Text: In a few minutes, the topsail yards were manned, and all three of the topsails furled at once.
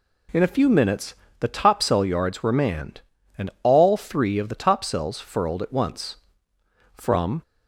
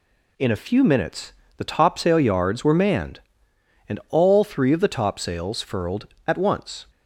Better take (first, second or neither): second